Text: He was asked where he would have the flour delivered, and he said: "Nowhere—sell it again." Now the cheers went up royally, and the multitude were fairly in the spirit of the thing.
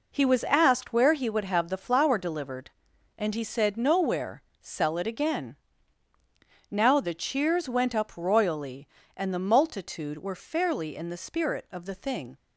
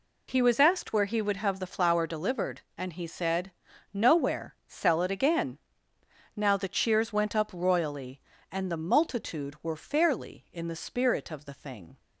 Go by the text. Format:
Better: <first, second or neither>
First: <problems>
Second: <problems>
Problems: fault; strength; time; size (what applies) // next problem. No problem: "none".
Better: neither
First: none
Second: none